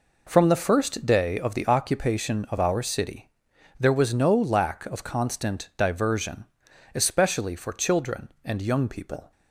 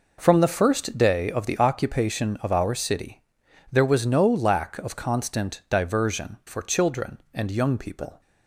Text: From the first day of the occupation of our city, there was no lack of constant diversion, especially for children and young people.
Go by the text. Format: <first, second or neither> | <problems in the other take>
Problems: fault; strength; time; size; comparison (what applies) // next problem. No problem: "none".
first | skips "especially"; at 6.4 s